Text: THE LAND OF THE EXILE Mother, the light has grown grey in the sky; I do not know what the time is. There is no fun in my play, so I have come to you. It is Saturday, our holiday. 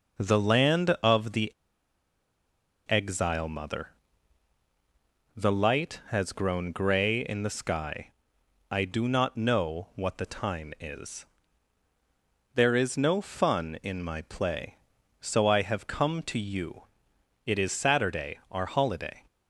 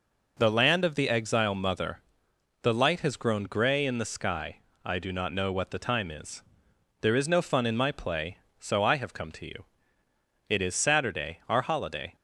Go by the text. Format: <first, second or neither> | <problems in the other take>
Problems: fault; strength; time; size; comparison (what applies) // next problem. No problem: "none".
second | pauses between "THE" and "EXILE"; strong; at 1.5 s; 1.3 s long